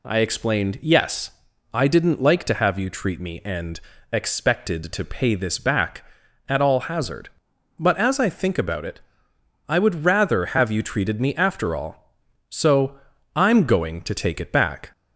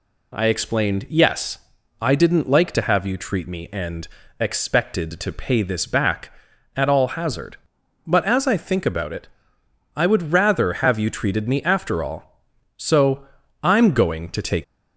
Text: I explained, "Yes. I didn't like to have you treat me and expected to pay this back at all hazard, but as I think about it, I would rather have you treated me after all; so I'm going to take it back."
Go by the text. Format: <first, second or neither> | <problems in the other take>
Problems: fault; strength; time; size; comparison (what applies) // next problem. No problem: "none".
first | pauses between "and" and "expected"; slight; at 4.0 s; 0.32 s long; slight in the first // pauses between "so" and "I'm"; slight; at 13.2 s; 0.34 s long; slight in the first // stops before "it back"; at 14.6 s